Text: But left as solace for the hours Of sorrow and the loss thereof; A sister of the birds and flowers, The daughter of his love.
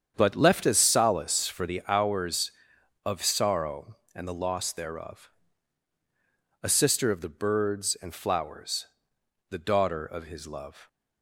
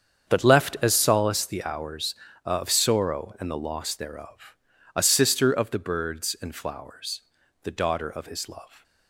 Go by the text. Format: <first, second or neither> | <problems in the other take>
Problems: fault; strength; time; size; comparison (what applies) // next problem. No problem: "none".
first | starts louder than the rest; strong; until 1.3 s; 7.5 dB; strong in the first // skips "for"; at 1.4 s